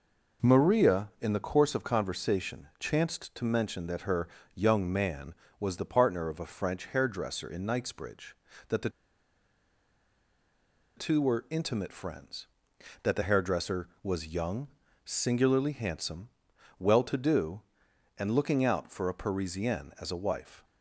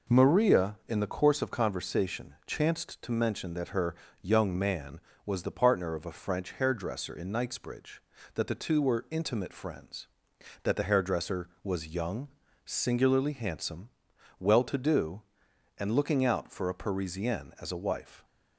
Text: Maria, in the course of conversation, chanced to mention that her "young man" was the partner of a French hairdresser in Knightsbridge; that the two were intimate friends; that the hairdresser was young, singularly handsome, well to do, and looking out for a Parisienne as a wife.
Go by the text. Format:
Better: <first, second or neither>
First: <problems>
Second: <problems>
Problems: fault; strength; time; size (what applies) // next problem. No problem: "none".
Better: second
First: pauses between "her" and "young"; slight; at 4.2 s; 0.28 s long // pauses between "the" and "two"; strong; at 8.8 s; 2.0 s long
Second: pauses between "her" and "young"; slight; at 3.9 s; 0.28 s long